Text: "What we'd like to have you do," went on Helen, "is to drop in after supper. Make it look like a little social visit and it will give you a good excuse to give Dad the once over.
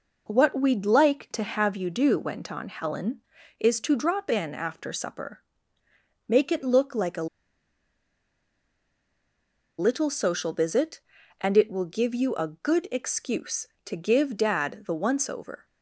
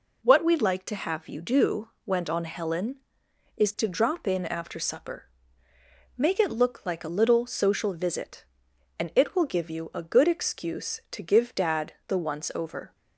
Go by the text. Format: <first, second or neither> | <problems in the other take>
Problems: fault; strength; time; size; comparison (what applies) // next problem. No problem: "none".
second | pauses between "a" and "little"; strong; at 7.2 s; 2.5 s long